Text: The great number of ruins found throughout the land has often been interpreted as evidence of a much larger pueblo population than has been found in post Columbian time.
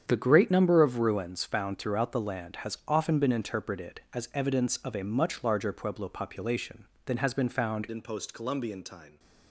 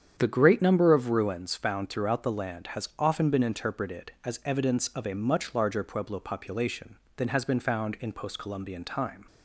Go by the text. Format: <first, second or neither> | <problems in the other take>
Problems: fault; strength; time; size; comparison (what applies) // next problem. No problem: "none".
second | starts louder than the rest; strong; until 1.0 s; 8 dB; strong in the second // changes voice at "in"; from 7.8 s on; 1.3 s long